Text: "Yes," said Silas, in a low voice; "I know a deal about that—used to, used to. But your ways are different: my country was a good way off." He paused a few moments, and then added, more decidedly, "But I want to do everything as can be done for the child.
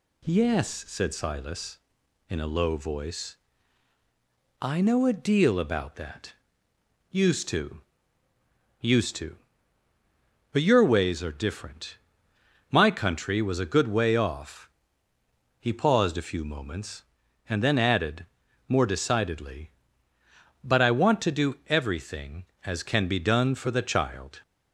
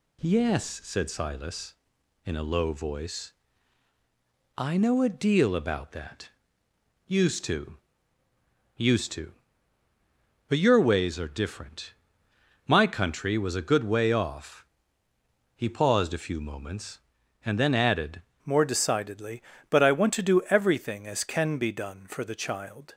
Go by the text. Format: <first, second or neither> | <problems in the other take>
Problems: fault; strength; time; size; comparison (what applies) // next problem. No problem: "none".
first | changes voice at "more"; from 18.4 s on; 4.5 s long